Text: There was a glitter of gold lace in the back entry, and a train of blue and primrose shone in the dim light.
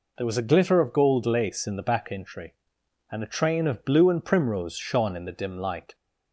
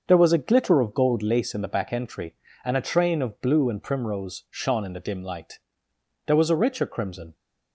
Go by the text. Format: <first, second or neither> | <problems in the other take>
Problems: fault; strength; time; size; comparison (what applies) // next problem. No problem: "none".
first | starts louder than the rest; until 1.0 s; 6.5 dB // goes on to say "There was a richer crimson"; noticeable; from 6.2 s on; 1.0 s long